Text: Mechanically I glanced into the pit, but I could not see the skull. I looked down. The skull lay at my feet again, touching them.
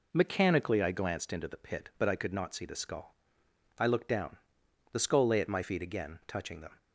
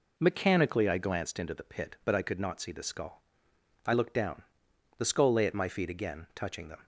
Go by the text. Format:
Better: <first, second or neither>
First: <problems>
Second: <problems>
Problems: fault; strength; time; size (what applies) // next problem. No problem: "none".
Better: neither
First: none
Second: none